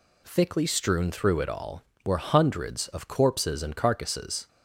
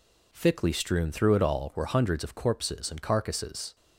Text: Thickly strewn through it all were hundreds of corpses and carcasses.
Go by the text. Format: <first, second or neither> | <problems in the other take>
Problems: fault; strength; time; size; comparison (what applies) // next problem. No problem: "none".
neither | none